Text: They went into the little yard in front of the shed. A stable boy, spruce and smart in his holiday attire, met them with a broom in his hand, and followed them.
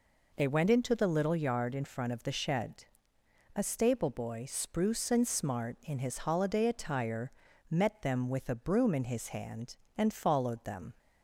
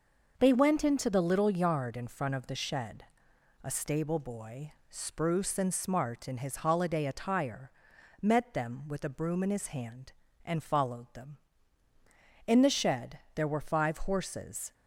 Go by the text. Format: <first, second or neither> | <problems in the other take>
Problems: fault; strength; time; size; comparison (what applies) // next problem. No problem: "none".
first | goes on to say "In the shed there were five horses"; strong; from 12.4 s on; 2.2 s long